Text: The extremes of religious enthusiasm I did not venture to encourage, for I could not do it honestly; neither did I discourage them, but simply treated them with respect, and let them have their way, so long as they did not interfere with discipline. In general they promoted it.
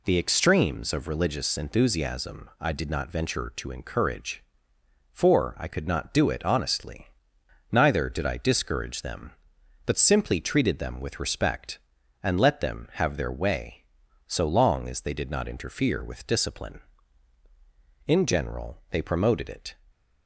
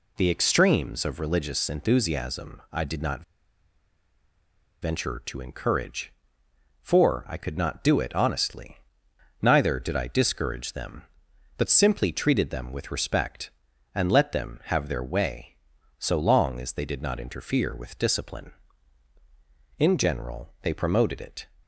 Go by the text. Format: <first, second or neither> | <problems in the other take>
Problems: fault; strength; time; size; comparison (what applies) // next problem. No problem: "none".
first | pauses between "not" and "venture"; strong; at 3.2 s; 1.5 s long